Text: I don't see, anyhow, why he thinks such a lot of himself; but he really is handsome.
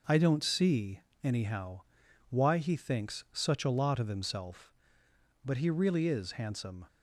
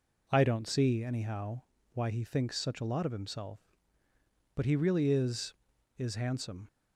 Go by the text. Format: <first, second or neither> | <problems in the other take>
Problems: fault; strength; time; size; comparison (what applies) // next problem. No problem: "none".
first | says "is" twice; at 5.9 s